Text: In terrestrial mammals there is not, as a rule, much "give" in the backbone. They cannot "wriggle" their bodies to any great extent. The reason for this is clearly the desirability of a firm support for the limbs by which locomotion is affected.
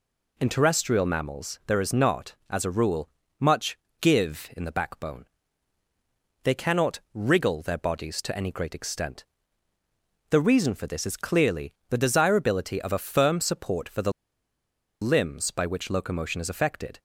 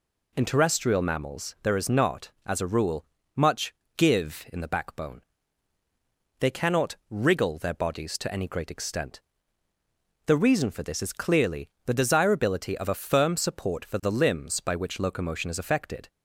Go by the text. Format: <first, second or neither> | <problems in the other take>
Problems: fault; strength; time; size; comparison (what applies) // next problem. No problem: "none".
second | pauses between "much" and "give"; slight; at 3.7 s; 0.22 s long; slight in the second // pauses between "cannot" and "wriggle"; slight; at 6.9 s; 0.16 s long; slight in the second // pauses between "clearly" and "the"; slight; at 11.7 s; 0.16 s long; slight in the second // pauses between "the" and "limbs"; noticeable; at 14.1 s; 0.90 s long